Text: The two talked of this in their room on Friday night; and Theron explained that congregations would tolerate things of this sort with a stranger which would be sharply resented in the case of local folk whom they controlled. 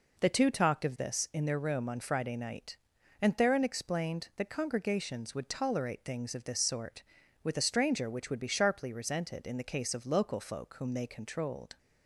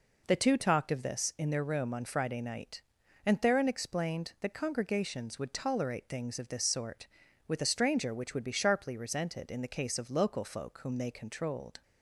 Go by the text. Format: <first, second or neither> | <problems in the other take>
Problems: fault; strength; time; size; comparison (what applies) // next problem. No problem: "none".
neither | none